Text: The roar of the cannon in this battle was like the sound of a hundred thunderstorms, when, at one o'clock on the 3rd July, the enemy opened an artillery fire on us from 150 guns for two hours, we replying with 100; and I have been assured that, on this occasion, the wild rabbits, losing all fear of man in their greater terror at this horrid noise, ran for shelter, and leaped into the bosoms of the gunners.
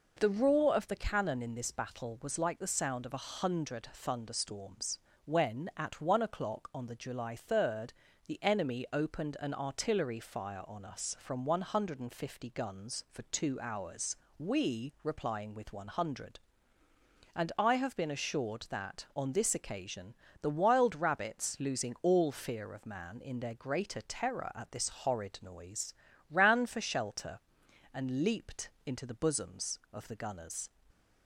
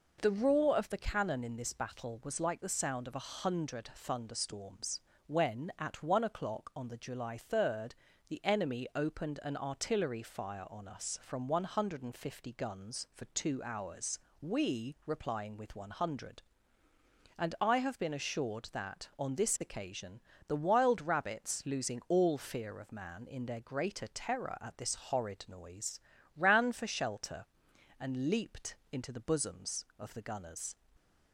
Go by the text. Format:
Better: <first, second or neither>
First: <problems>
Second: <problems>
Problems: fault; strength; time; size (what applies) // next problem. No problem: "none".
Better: neither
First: pauses between "leaped" and "into"; slight; at 28.6 s; 0.16 s long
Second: pauses between "leaped" and "into"; slight; at 28.7 s; 0.16 s long